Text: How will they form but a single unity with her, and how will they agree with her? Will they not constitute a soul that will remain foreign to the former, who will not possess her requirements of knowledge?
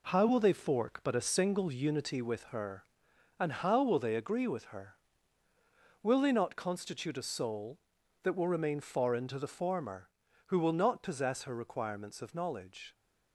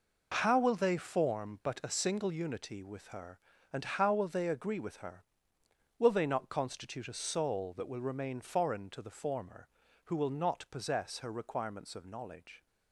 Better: second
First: says "fork" for "form"; at 0.5 s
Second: none

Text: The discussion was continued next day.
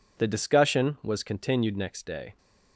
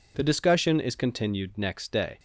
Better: first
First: none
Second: says "is" for "was"; at 0.7 s

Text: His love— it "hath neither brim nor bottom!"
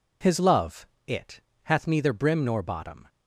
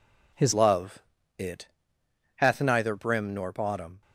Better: first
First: pauses between "it" and "hath"; slight; at 1.4 s; 0.22 s long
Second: changes voice at "love"; from 0.5 s on; 3.5 s long // pauses between "it" and "hath"; noticeable; at 1.6 s; 0.70 s long

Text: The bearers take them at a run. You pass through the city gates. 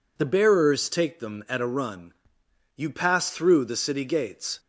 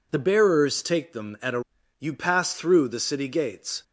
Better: first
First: none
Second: skips "run"; at 1.8 s

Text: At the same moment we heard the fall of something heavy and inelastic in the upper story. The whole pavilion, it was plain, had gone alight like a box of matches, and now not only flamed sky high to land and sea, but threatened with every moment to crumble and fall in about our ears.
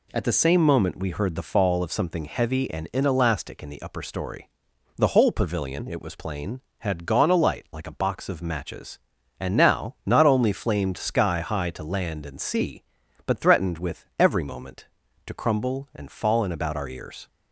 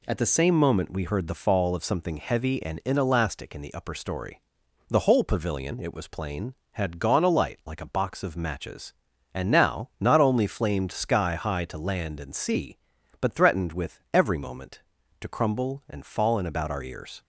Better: neither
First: none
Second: none

